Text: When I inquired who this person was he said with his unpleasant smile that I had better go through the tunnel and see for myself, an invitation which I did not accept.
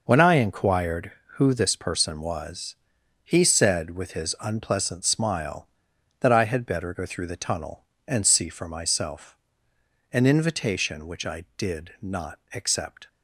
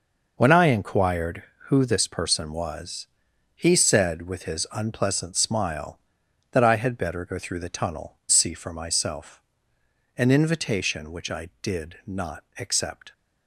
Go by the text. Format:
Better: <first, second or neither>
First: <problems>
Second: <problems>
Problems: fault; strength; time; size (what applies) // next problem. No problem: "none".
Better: first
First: pauses between "was" and "he"; noticeable; at 2.7 s; 0.48 s long // pauses between "not" and "accept"; slight; at 12.3 s; 0.16 s long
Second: pauses between "was" and "he"; noticeable; at 3.0 s; 0.48 s long // skips "and"; at 8.2 s // pauses between "not" and "accept"; slight; at 12.4 s; 0.16 s long